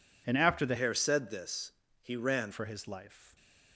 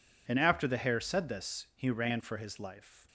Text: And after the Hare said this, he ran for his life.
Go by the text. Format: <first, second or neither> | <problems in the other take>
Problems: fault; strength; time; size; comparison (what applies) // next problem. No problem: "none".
second | changes voice from "Hare" to "ran"; from 0.7 to 2.5 s; 1.8 s long